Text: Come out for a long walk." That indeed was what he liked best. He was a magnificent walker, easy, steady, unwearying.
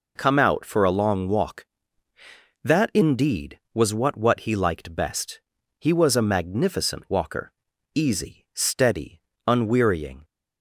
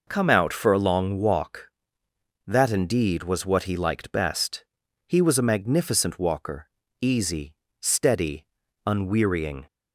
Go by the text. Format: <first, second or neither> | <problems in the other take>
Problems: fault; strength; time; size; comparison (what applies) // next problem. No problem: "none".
second | says "what" twice; at 4.1 s